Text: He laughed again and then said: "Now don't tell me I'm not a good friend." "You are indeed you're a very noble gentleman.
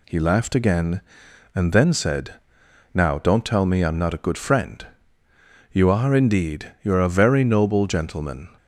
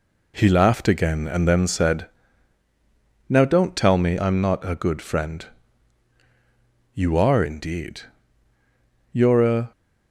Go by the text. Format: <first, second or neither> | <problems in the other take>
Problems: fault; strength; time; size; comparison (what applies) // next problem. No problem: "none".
first | pauses between "indeed" and "you're"; at 8.0 s; 1.0 s long // stops before "very noble gentleman"; at 9.7 s